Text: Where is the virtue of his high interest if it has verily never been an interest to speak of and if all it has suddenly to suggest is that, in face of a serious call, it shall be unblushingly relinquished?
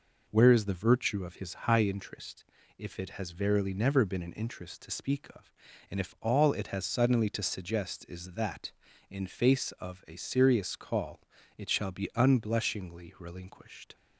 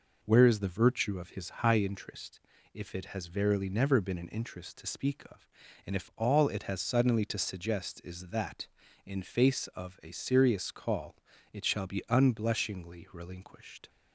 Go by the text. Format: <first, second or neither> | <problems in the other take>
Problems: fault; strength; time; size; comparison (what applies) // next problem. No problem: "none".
neither | pauses between "interest" and "if"; slight; the same in both